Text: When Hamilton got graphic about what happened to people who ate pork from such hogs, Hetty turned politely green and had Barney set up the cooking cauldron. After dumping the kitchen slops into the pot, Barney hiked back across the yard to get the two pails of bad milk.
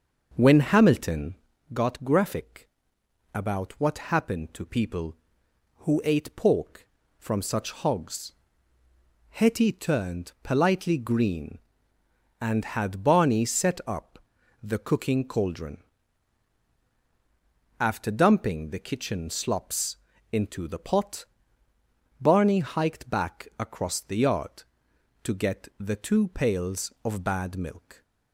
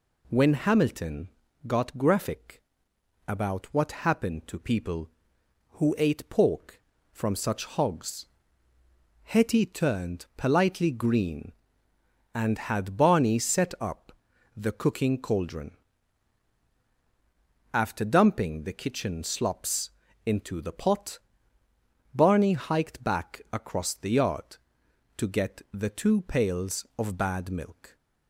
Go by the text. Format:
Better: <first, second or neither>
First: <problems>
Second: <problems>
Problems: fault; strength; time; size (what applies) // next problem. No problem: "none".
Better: second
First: starts louder than the rest; until 1.5 s; 6 dB // pauses between "Hamilton" and "got"; at 1.3 s; 0.40 s long // pauses between "graphic" and "about"; noticeable; at 2.6 s; 0.68 s long // pauses between "up" and "the"; at 14.1 s; 0.44 s long // pauses between "slops" and "into"; slight; at 19.9 s; 0.34 s long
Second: pauses between "Hamilton" and "got"; at 1.2 s; 0.40 s long // pauses between "graphic" and "about"; noticeable; at 2.5 s; 0.68 s long // pauses between "up" and "the"; at 14.1 s; 0.44 s long // pauses between "slops" and "into"; slight; at 19.8 s; 0.34 s long